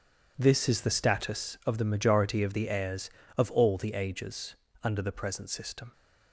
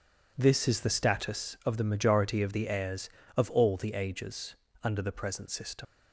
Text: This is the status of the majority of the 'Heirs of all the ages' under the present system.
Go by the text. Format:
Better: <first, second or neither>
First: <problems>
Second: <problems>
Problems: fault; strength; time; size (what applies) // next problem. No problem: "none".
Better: first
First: pauses between "ages" and "under"; slight; at 4.5 s; 0.26 s long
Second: pauses between "ages" and "under"; slight; at 4.5 s; 0.26 s long // leaves "system" unfinished; at 5.8 s; 80 ms